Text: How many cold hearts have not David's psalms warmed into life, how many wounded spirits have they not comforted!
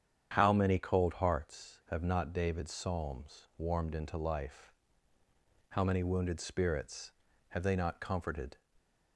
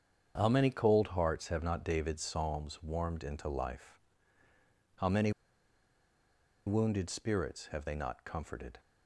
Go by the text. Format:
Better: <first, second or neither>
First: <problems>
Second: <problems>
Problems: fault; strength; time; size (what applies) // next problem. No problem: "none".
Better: first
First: starts louder than the rest; strong; until 1.3 s; 8.5 dB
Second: starts louder than the rest; strong; until 1.3 s; 7.5 dB // pauses between "many" and "wounded"; strong; at 5.3 s; 1.3 s long